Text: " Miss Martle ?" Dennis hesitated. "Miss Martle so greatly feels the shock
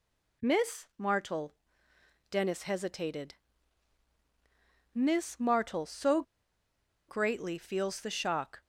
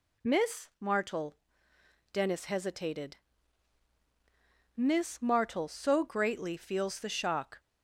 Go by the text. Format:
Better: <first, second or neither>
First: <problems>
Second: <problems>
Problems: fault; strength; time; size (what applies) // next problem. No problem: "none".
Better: second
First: pauses between "so" and "greatly"; noticeable; at 6.2 s; 0.86 s long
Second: none